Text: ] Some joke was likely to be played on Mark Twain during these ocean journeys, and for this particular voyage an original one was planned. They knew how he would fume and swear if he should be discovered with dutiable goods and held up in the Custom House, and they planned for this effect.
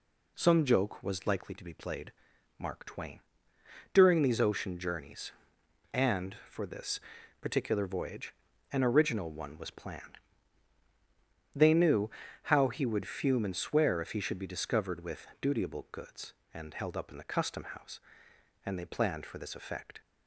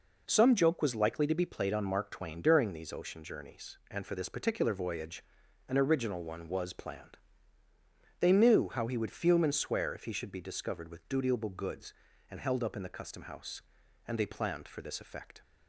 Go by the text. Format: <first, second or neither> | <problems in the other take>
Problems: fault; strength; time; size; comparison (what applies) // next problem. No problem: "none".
second | skips "on"; at 2.3 s // pauses between "Twain" and "during"; noticeable; at 3.2 s; 0.72 s long // pauses between "this" and "particular"; at 6.9 s; 0.42 s long // pauses between "voyage" and "an"; at 8.3 s; 0.38 s long; noticeable in the second // pauses between "knew" and "how"; slight; at 12.1 s; 0.34 s long